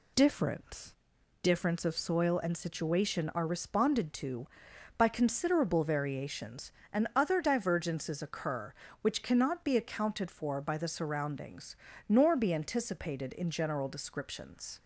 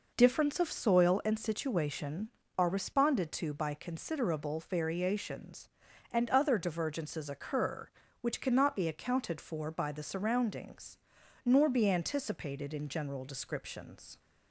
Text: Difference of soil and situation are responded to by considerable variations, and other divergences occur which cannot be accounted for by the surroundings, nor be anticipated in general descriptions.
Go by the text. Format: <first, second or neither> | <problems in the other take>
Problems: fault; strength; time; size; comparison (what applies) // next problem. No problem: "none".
second | says "Difference" twice; at 1.4 s